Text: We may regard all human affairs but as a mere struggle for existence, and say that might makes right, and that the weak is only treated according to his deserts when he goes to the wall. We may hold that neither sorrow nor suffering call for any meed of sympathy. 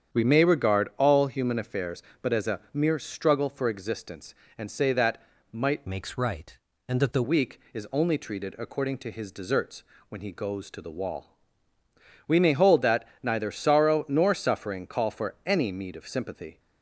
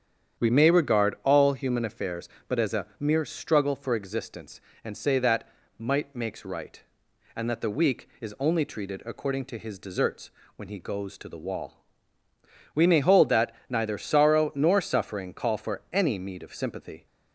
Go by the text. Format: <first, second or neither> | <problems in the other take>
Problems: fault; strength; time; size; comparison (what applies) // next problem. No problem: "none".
second | starts louder than the rest; strong; until 1.2 s; 8 dB; strong in the second // pauses between "that" and "might"; slight; at 5.2 s; 0.30 s long; slight in the second // changes voice from "makes" to "the"; from 5.8 to 7.2 s; 1.4 s long // pauses between "deserts" and "when"; slight; at 9.8 s; 0.26 s long; slight in the second // pauses between "that" and "neither"; slight; at 13.0 s; 0.16 s long; slight in the second